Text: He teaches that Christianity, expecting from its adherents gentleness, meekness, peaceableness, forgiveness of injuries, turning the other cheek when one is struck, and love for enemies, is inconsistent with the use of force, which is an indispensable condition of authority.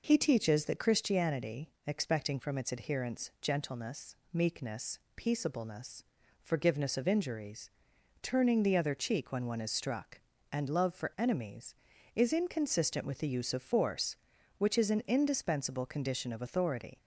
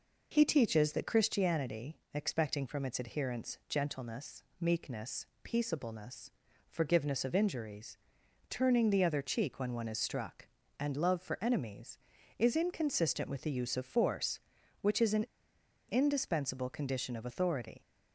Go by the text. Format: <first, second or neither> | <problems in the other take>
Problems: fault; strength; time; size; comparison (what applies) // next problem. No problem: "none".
first | pauses between "an" and "indispensable"; noticeable; at 15.2 s; 0.64 s long